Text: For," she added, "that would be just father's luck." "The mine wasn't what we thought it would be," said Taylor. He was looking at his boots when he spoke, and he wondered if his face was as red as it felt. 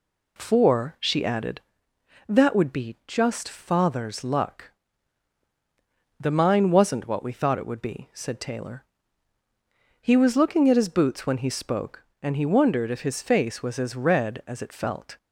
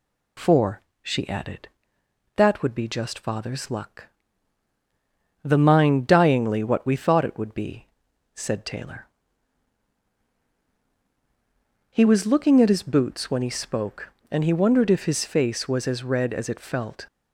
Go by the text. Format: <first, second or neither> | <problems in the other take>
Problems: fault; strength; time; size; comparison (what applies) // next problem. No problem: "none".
first | says "dyingly" for "wasn't"; at 6.0 s